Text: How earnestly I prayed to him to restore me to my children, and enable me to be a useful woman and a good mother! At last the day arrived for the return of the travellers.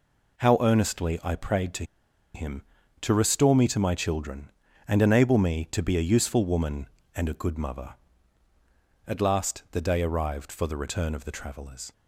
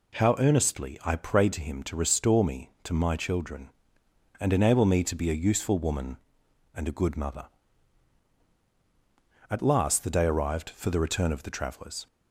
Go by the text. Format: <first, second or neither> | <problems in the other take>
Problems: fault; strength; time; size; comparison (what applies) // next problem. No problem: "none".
second | pauses between "to" and "him"; noticeable; at 1.8 s; 0.50 s long